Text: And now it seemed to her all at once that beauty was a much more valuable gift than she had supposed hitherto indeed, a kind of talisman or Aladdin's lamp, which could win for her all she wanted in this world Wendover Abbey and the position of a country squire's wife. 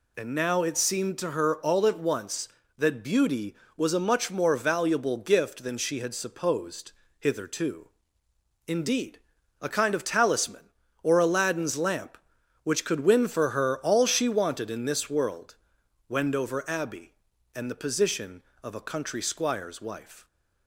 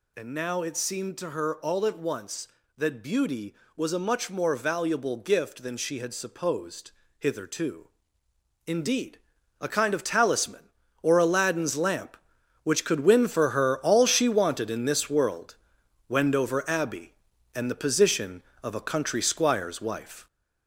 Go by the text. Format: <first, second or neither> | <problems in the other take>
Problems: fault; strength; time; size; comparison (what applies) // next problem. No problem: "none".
first | gets louder; throughout; 3.5 dB // pauses between "supposed" and "hitherto"; slight; at 6.9 s; 0.26 s long; slight in the first // pauses between "hitherto" and "indeed"; noticeable; at 7.8 s; 0.78 s long; noticeable in the first // pauses between "world" and "Wendover"; noticeable; at 15.5 s; 0.52 s long; noticeable in the first